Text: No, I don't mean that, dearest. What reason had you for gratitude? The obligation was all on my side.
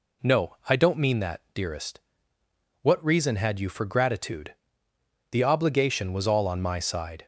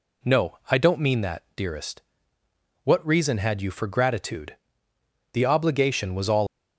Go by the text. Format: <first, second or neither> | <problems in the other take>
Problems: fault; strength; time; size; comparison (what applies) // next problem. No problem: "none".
first | stops before "on my side"; at 6.4 s